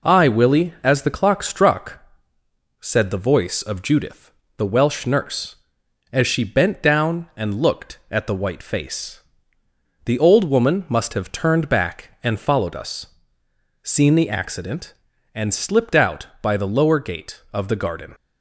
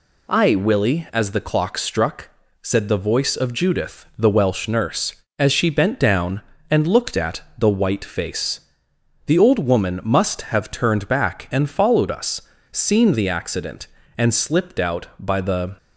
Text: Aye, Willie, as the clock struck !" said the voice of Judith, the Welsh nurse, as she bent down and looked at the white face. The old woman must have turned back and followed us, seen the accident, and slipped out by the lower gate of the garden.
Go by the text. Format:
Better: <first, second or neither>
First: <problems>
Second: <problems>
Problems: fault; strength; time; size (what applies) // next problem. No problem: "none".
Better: first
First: none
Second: pauses between "at" and "the"; slight; at 7.4 s; 0.16 s long // stops before "lower gate of the garden"; at 15.7 s